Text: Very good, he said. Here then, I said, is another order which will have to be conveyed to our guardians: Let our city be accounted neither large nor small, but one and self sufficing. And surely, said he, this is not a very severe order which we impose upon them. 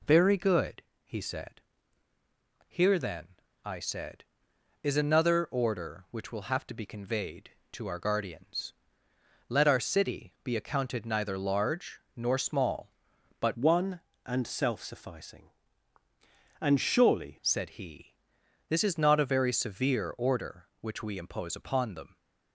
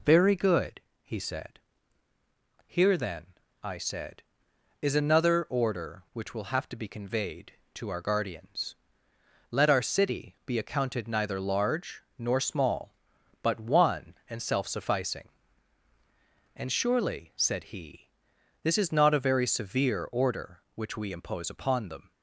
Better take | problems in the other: second | pauses between "large" and "nor"; slight; at 12.0 s; 0.16 s long; slight in the second // changes voice from "one" to "surely"; from 13.5 to 17.3 s; 3.8 s long

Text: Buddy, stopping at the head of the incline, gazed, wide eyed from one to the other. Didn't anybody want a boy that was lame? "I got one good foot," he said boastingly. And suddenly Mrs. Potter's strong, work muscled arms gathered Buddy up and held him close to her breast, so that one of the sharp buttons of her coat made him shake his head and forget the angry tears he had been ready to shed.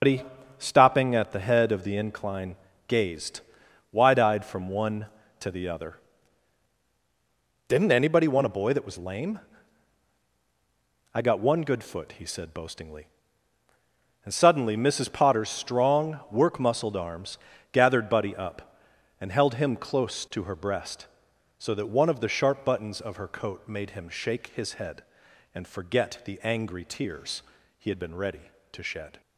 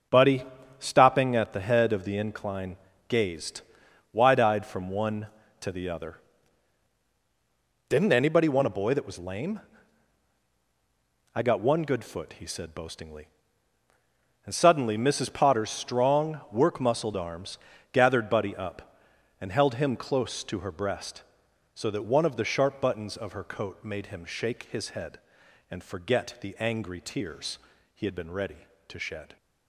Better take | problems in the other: second | loses the start of "Buddy"; at 0.0 s; 125 ms // starts louder than the rest; until 1.3 s; 7 dB; strong in the second // pauses between "arms" and "gathered"; slight; at 17.3 s; 0.34 s long; slight in the second // pauses between "tears" and "he"; slight; at 27.4 s; 0.34 s long; slight in the second

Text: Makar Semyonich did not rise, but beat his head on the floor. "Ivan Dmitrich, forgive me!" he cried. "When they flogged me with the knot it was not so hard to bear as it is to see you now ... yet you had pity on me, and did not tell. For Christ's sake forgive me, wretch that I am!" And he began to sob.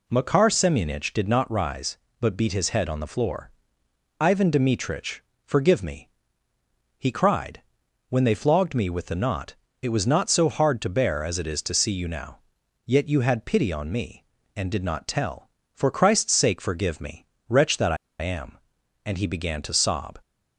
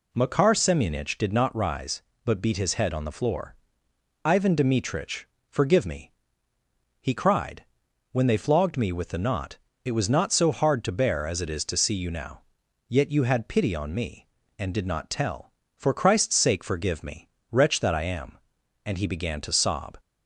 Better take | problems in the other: second | pauses between "knot" and "it"; slight; at 9.5 s; 0.26 s long; slight in the second // pauses between "I" and "am"; slight; at 17.9 s; 0.24 s long

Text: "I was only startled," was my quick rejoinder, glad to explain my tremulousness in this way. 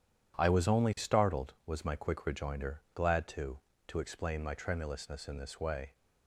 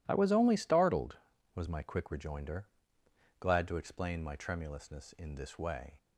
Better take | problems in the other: second | says "to" twice; at 3.8 s

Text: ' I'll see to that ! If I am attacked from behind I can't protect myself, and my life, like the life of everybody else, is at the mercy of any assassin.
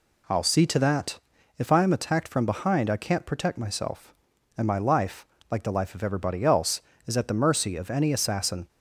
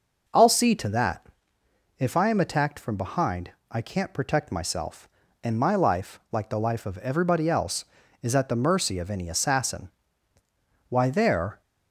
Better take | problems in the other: first | pauses between "behind" and "I"; slight; at 3.5 s; 0.18 s long // goes on to say "Why there"; noticeable; from 10.8 s on; 0.72 s long

